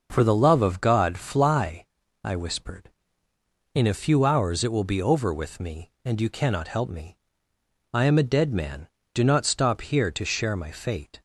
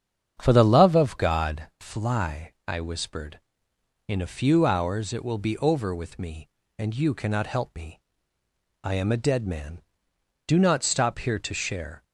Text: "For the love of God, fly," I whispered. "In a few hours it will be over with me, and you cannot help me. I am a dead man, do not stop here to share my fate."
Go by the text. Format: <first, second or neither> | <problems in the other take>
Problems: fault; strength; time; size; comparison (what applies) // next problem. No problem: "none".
first | starts louder than the rest; strong; until 1.3 s; 8 dB // stops before "my fate"; at 12.0 s